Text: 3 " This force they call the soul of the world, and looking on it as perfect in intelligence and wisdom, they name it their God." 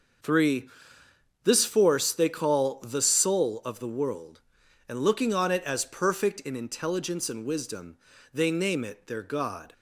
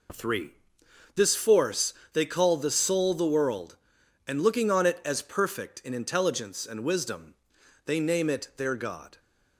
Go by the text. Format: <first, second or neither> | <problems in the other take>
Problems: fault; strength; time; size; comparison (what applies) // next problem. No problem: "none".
first | pauses between "force" and "they"; slight; at 1.9 s; 0.22 s long // skips "of"; at 3.1 s